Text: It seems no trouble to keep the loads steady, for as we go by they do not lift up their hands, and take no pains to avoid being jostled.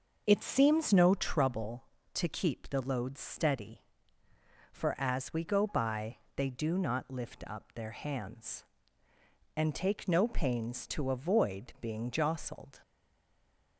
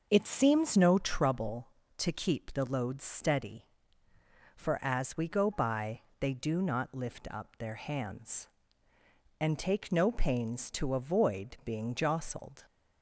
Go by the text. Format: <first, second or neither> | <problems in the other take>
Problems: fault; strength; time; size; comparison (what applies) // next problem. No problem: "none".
second | starts louder than the rest; noticeable; until 1.2 s; 6 dB; noticeable in the second // pauses between "by" and "they"; slight; at 6.1 s; 0.18 s long; slight in the second // stays silent after the last word; slight; from 12.8 s on; 0.9 s long